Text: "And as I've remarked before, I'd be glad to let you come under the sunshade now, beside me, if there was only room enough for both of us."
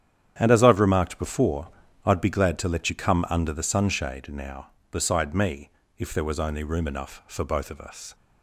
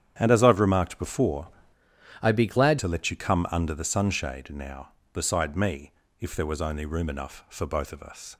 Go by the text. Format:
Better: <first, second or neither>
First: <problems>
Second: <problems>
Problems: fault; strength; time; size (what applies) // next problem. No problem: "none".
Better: first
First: starts louder than the rest; strong; until 1.3 s; 9.5 dB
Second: starts louder than the rest; strong; until 1.1 s; 9.5 dB // changes voice from "I'd" to "glad"; from 2.2 to 2.7 s; 0.5 s long